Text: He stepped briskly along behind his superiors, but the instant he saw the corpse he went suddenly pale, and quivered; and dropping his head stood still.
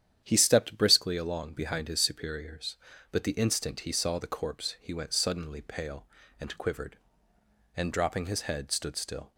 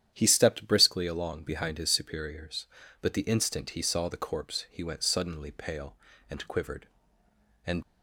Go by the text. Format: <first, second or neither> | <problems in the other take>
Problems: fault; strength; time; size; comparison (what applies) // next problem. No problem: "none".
first | starts louder than the rest; strong; until 1.1 s; 10 dB; strong in the first // stops before "dropping his head stood still"; at 7.8 s